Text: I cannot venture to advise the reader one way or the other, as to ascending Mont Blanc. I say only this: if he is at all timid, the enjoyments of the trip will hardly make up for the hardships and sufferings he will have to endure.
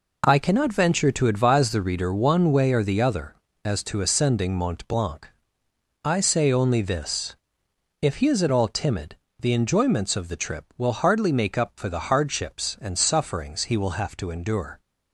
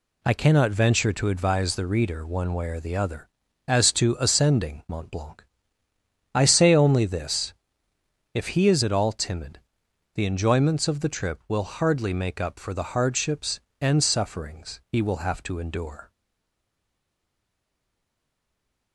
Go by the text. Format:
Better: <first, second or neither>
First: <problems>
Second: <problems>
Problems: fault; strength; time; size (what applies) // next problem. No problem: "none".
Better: first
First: none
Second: stays silent after the last word; strong; from 16.0 s on; 2.9 s long